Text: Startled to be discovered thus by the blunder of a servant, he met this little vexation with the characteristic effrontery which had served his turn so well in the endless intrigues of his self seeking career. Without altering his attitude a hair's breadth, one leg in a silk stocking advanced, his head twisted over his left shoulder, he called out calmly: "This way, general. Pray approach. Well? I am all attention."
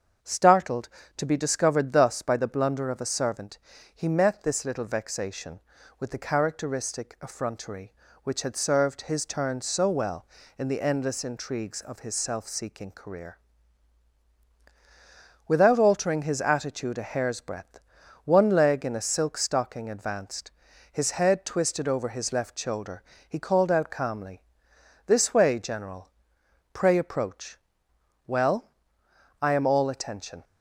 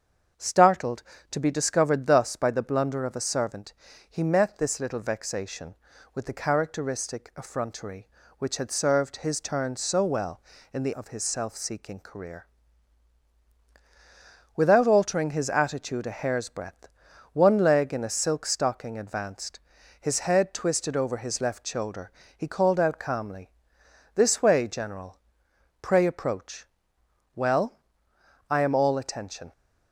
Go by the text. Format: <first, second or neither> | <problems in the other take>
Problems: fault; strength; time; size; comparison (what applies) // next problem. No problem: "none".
first | starts louder than the rest; strong; until 1.6 s; 7 dB; strong in the first // skips "endless intrigues"; at 10.9 s